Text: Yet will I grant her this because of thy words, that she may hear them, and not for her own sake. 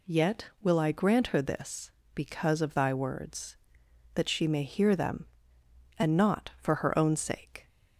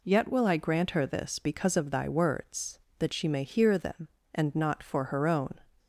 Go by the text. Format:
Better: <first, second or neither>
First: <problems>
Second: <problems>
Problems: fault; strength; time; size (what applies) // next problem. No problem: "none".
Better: first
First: none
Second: stops before "sake"; at 5.7 s